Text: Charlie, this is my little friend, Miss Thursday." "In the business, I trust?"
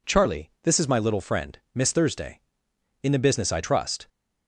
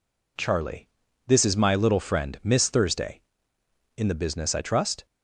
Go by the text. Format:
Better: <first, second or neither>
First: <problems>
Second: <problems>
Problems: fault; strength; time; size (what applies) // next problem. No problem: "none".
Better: neither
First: none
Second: none